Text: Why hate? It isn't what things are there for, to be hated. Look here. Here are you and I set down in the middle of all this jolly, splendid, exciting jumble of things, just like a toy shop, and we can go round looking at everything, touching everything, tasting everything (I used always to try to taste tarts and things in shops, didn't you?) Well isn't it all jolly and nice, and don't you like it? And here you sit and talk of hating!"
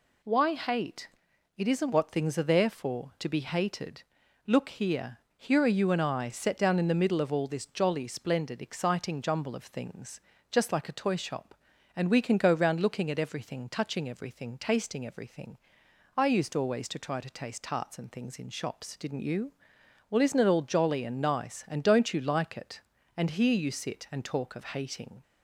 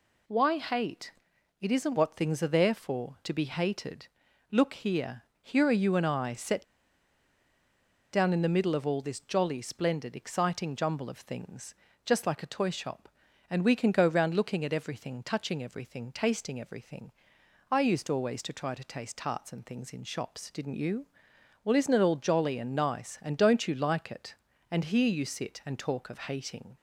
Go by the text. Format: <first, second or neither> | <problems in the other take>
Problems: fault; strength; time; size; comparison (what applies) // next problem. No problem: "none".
first | pauses between "set" and "down"; strong; at 6.6 s; 1.4 s long